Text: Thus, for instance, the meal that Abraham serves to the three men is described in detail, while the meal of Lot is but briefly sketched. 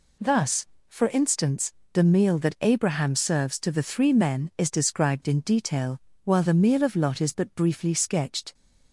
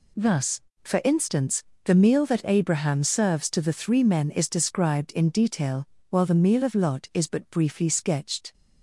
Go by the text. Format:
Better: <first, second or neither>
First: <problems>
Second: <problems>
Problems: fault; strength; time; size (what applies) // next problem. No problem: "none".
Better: neither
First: none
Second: none